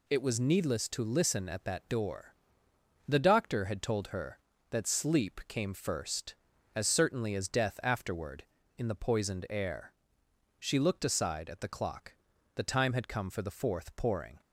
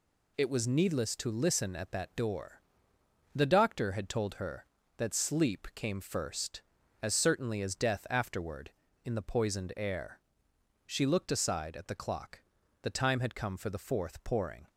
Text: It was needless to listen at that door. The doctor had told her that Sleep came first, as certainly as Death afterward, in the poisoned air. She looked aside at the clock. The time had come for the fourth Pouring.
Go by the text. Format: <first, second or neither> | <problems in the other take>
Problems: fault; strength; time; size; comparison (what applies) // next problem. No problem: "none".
neither | none